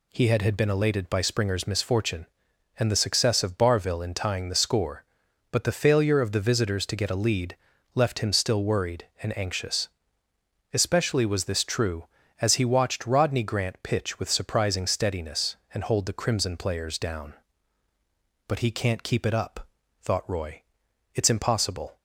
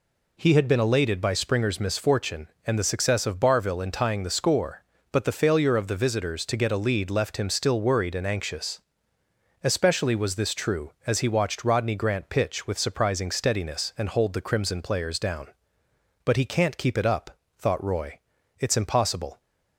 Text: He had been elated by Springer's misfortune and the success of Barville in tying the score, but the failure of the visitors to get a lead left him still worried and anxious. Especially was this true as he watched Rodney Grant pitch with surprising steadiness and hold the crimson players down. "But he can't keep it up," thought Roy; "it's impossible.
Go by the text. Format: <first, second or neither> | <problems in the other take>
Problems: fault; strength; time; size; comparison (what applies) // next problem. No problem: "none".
second | says "had" twice; at 0.4 s // pauses between "lead" and "left"; at 7.5 s; 0.38 s long